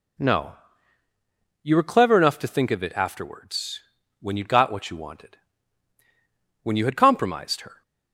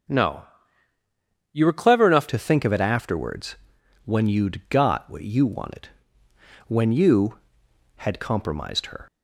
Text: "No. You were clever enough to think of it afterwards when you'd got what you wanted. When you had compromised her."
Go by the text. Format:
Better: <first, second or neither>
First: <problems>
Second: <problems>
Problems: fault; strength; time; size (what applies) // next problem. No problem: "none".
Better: first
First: pauses between "afterwards" and "when"; at 3.8 s; 0.38 s long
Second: starts louder than the rest; until 2.1 s; 6.5 dB // changes voice at "to"; from 2.2 s on; 6.8 s long // pauses between "afterwards" and "when"; noticeable; at 3.5 s; 0.48 s long